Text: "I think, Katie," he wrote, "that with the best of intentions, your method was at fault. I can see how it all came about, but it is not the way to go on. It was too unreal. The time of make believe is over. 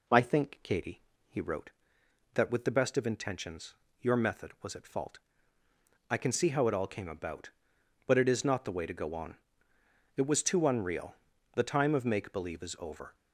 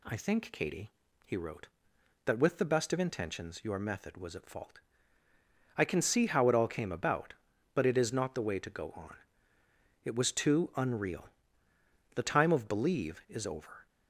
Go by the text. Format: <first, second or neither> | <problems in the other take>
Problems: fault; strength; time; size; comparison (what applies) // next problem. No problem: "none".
first | skips "make"; at 12.6 s